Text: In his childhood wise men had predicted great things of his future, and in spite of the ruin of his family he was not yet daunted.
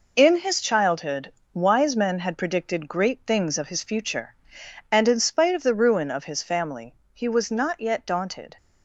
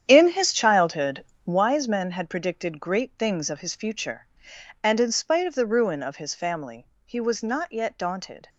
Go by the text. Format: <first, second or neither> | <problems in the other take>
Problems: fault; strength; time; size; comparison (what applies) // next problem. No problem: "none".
first | starts louder than the rest; strong; until 1.6 s; 9 dB // pauses between "childhood" and "wise"; slight; at 1.2 s; 0.20 s long; slight in the first // pauses between "family" and "he"; slight; at 6.8 s; 0.18 s long; slight in the first